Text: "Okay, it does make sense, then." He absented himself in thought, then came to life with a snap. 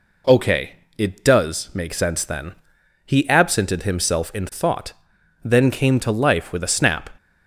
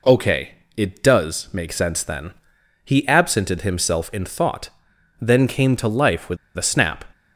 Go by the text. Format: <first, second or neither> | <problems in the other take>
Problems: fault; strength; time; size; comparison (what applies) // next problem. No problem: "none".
first | pauses between "with" and "a"; slight; at 6.3 s; 0.19 s long